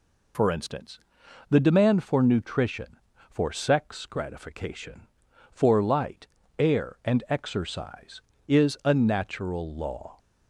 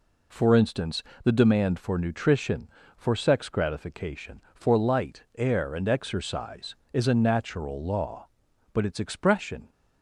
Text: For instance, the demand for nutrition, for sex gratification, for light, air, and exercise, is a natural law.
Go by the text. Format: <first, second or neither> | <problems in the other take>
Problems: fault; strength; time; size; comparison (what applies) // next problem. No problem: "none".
first | goes on to say "But its expression"; noticeable; from 8.7 s on; 1.0 s long